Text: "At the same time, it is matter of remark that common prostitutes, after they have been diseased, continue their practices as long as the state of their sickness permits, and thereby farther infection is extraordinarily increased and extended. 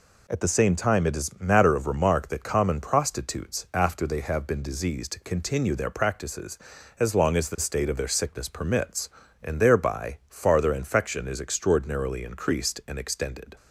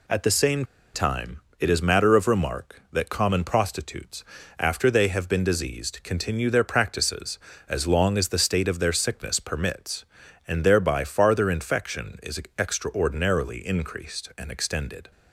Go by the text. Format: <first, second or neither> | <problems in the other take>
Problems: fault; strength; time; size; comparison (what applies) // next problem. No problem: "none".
first | pauses between "same" and "time"; slight; at 0.6 s; 0.29 s long // pauses between "is" and "extraordinarily"; slight; at 12.4 s; 0.16 s long